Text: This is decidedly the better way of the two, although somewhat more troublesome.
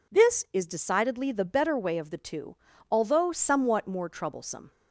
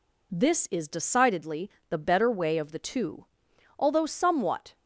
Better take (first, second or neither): first